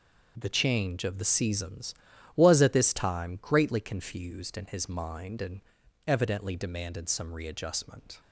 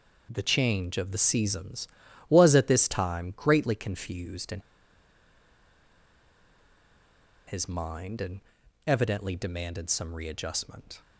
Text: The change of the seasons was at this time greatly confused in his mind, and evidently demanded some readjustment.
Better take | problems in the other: first | pauses between "in" and "his"; strong; at 4.5 s; 2.8 s long // pauses between "and" and "evidently"; noticeable; at 8.4 s; 0.46 s long; noticeable in the first

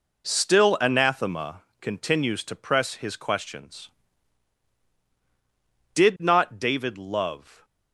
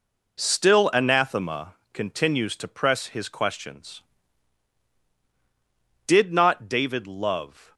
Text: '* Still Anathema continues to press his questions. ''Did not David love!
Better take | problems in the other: neither | pauses between "Anathema" and "continues"; slight; the same in both

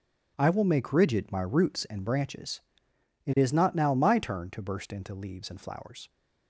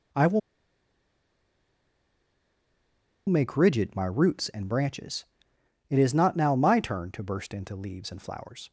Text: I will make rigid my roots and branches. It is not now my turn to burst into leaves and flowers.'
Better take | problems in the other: first | pauses between "will" and "make"; strong; at 0.3 s; 2.8 s long

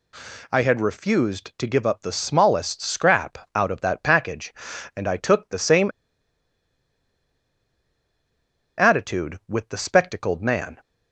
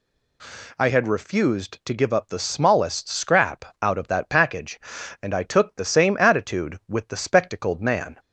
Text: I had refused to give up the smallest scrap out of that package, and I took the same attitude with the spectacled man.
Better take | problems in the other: second | pauses between "scrap" and "out"; slight; at 3.3 s; 0.20 s long; slight in the second // pauses between "same" and "attitude"; strong; at 5.9 s; 2.8 s long

